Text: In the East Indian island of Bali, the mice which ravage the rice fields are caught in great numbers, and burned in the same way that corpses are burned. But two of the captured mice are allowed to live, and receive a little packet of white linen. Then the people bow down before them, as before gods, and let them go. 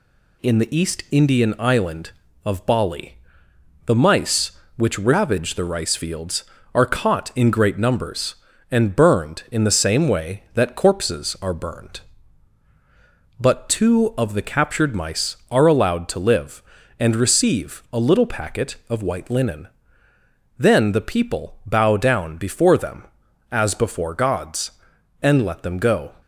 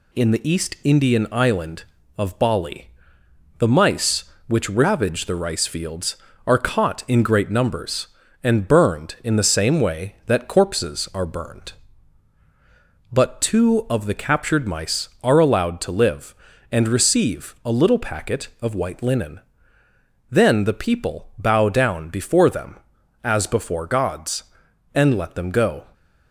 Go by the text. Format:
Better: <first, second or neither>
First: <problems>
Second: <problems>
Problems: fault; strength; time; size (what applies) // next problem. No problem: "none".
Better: neither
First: none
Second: none